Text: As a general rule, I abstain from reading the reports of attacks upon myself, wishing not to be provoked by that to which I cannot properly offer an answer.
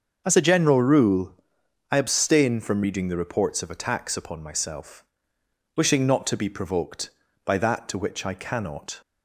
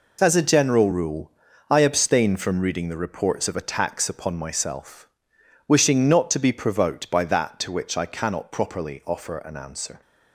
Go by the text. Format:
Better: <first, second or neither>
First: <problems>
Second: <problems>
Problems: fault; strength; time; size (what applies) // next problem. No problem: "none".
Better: second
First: starts louder than the rest; until 1.2 s; 6.5 dB // stops before "properly offer an answer"; at 9.0 s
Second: none